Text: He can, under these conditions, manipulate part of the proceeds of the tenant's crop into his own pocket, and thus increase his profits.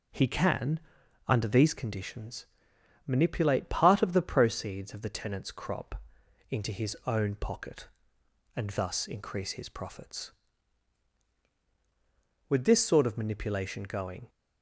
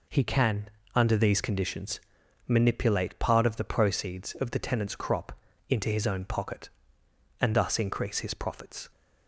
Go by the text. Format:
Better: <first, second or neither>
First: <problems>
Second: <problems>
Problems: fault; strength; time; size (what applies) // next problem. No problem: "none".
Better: second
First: pauses between "crop" and "into"; noticeable; at 6.0 s; 0.48 s long // goes on to say "With this sort of manipulation going"; strong; from 12.4 s on; 1.8 s long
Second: pauses between "crop" and "into"; slight; at 5.3 s; 0.36 s long